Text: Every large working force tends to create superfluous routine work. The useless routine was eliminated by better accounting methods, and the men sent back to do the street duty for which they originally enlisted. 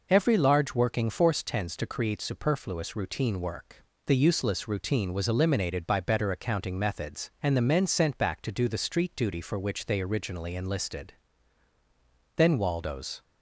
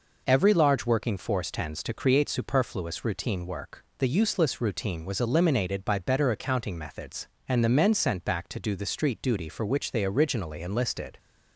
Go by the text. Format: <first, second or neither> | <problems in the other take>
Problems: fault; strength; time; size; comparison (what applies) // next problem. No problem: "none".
second | goes on to say "Then Waldo's"; noticeable; from 12.3 s on; 0.86 s long